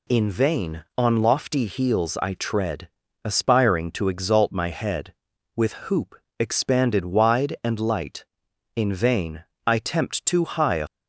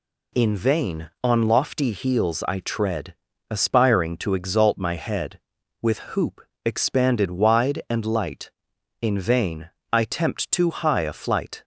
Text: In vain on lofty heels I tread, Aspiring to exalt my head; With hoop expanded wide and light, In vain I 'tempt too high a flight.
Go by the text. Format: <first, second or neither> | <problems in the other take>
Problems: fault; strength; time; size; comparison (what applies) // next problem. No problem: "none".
second | pauses between "hoop" and "expanded"; slight; at 6.1 s; 0.24 s long; slight in the second // pauses between "vain" and "I"; slight; at 9.4 s; 0.22 s long; slight in the second // stops before "flight"; at 10.8 s